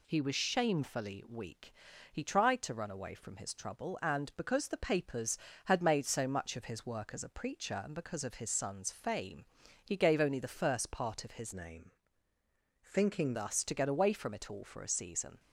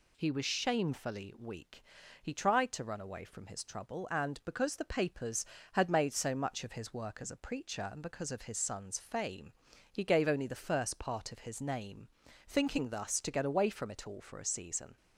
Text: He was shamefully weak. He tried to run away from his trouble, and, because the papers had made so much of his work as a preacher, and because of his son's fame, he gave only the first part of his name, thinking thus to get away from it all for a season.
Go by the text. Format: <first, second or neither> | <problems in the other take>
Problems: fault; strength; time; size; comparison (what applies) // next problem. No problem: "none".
second | changes voice from "name" to "thinking"; from 11.5 to 13.3 s; 1.8 s long